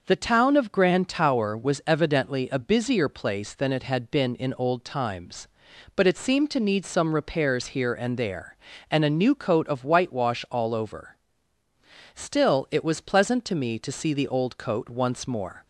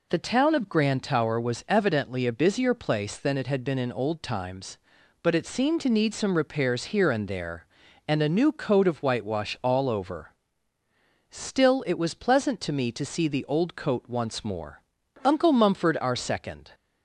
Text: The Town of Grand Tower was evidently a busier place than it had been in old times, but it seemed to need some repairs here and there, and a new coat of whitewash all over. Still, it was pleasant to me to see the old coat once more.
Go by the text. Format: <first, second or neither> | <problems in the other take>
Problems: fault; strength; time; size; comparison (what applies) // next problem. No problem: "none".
first | goes on to say "Uncle Mumford our second"; from 15.2 s on; 1.4 s long